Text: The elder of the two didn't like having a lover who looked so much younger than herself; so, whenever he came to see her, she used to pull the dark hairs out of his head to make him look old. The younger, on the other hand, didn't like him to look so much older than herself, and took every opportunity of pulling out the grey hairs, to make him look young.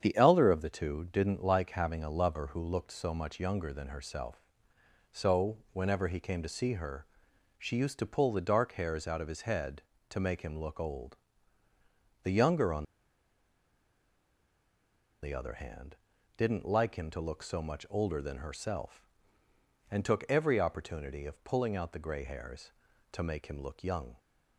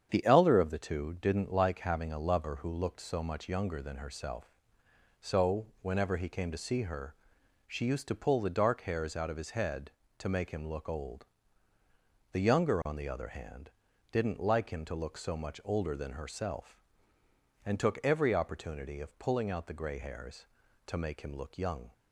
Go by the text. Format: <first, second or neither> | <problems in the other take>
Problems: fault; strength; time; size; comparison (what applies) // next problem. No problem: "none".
second | starts louder than the rest; strong; until 1.0 s; 8 dB; strong in the second // pauses between "on" and "the"; strong; at 12.8 s; 2.3 s long